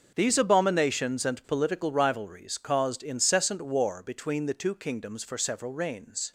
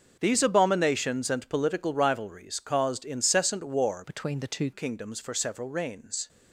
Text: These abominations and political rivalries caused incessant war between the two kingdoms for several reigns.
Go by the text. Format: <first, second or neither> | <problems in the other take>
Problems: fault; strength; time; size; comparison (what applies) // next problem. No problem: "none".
first | starts louder than the rest; until 1.2 s; 6 dB; noticeable in the first // changes voice from "between" to "two"; from 4.0 to 4.7 s; 0.7 s long